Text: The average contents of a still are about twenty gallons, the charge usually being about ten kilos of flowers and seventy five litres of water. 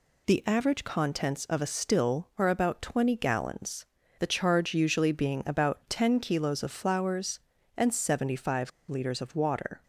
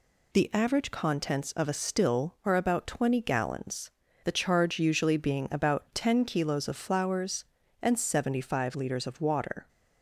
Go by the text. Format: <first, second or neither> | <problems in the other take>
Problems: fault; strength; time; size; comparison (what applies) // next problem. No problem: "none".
second | pauses between "five" and "litres"; slight; at 8.7 s; 0.17 s long